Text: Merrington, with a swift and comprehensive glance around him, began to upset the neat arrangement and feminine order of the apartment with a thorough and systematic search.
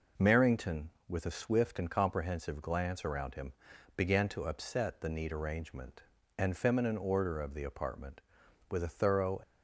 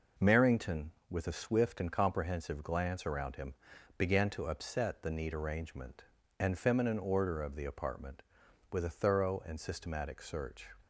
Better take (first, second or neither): second